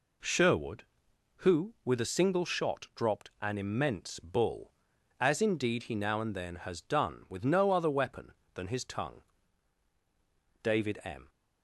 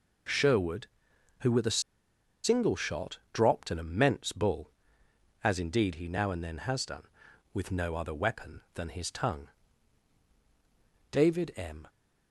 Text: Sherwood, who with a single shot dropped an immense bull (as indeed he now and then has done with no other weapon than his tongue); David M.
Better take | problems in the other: first | pauses between "a" and "single"; noticeable; at 1.8 s; 0.62 s long

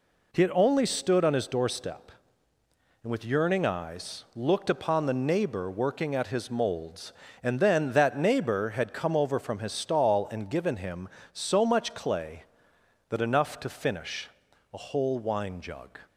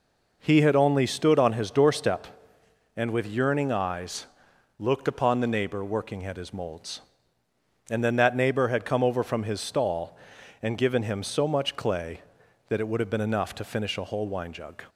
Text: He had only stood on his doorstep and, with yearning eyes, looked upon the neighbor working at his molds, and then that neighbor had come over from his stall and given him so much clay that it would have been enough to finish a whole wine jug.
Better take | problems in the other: second | skips "it would have been"; at 13.2 s // pauses between "finish" and "a"; at 14.2 s; 0.44 s long

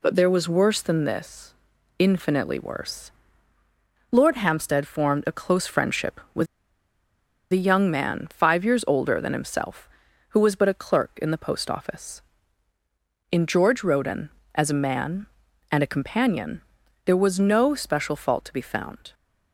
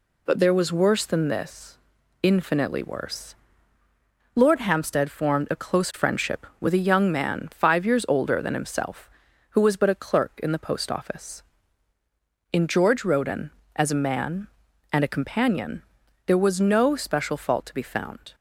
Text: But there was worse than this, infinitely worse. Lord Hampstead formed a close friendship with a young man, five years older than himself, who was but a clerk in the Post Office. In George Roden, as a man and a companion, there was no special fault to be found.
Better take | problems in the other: second | pauses between "with" and "a"; at 6.4 s; 1.0 s long

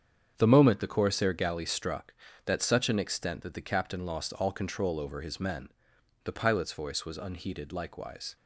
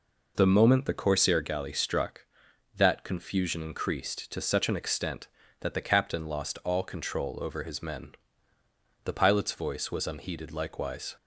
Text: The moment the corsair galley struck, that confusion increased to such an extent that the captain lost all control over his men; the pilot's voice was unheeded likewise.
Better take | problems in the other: second | starts louder than the rest; strong; until 1.3 s; 8 dB // skips "confusion increased to"; at 2.6 s

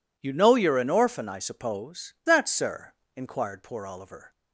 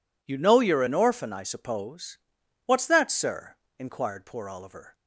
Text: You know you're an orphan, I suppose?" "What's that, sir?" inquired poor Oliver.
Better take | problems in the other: second | skips "What's"; at 2.2 s

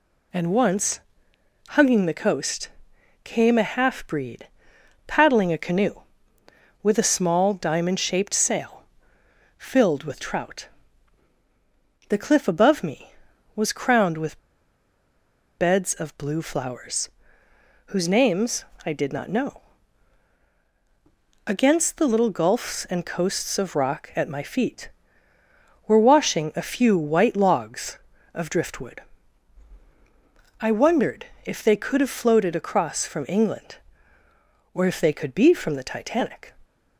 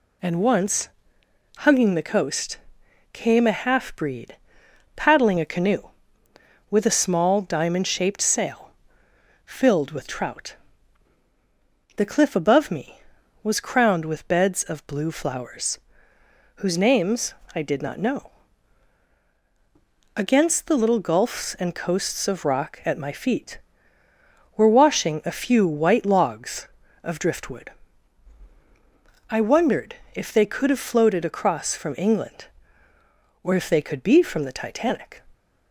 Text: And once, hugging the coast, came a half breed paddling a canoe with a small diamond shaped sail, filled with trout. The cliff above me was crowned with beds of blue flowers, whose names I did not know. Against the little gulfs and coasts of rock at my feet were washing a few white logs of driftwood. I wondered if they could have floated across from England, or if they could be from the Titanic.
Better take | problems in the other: second | pauses between "breed" and "paddling"; noticeable; at 4.4 s; 0.60 s long; noticeable in the second // pauses between "with" and "beds"; at 14.3 s; 1.1 s long // pauses between "names" and "I"; slight; at 18.6 s; 0.22 s long; slight in the second // pauses between "wondered" and "if"; slight; at 31.2 s; 0.20 s long; slight in the second

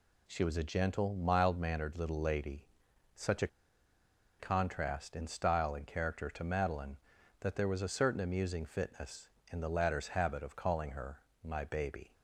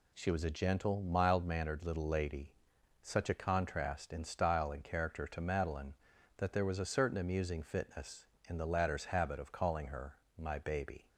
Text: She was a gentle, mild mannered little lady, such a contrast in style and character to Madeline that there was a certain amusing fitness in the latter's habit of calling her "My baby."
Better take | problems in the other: second | pauses between "a" and "contrast"; noticeable; at 3.4 s; 0.92 s long // pauses between "her" and "My"; slight; at 11.1 s; 0.24 s long; slight in the second

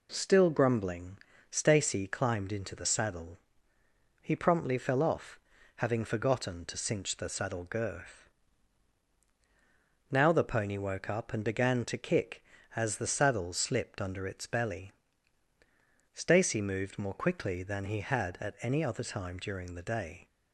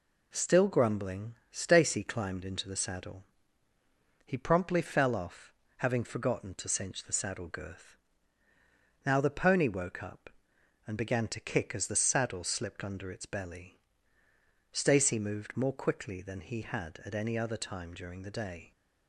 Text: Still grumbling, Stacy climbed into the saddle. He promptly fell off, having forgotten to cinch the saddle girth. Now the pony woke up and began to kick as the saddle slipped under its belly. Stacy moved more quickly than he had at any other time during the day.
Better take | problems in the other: neither | none

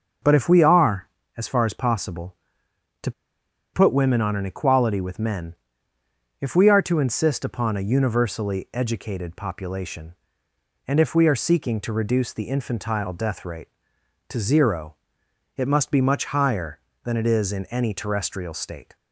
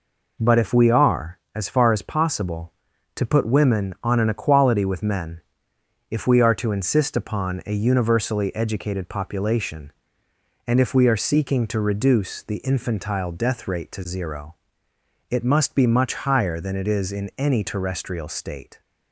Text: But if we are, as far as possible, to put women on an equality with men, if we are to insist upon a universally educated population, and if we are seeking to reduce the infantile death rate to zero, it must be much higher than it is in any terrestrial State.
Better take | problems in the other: second | starts louder than the rest; until 1.5 s; 6.5 dB // pauses between "to" and "put"; noticeable; at 3.1 s; 0.62 s long

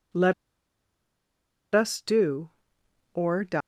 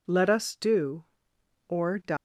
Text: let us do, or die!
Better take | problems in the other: second | pauses between "let" and "us"; strong; at 0.3 s; 1.4 s long

